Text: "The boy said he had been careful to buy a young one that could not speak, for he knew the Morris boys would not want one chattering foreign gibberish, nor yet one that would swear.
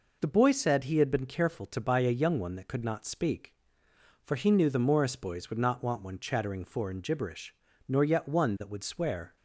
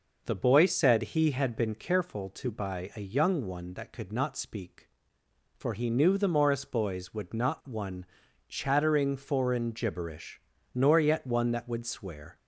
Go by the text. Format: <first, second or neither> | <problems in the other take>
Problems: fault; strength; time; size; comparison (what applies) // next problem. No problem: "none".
first | skips "want"; at 7.6 s // pauses between "one" and "chattering"; noticeable; at 8.0 s; 0.46 s long